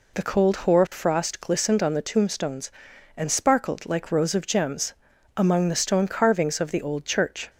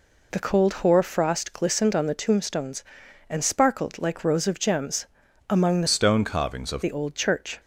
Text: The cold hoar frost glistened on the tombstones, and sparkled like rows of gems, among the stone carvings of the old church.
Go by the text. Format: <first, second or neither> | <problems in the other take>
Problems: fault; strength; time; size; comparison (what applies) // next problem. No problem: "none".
first | changes voice from "stone" to "of"; from 5.8 to 6.8 s; 1.0 s long